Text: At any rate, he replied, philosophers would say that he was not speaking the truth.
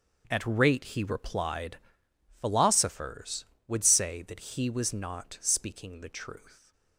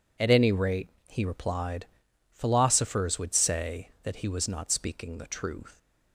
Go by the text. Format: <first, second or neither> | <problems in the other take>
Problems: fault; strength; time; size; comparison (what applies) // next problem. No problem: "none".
second | starts louder than the rest; until 1.3 s; 6.5 dB // skips "any"; at 0.4 s